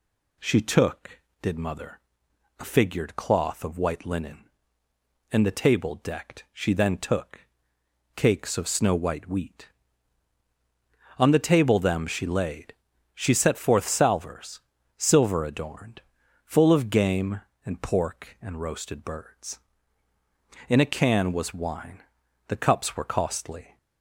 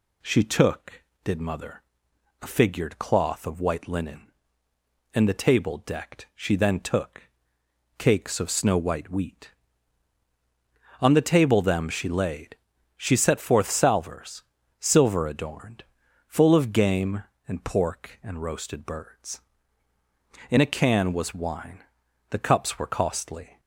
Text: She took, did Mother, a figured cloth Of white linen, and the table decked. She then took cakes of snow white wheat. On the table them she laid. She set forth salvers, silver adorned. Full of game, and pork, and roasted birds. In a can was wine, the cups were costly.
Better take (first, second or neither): neither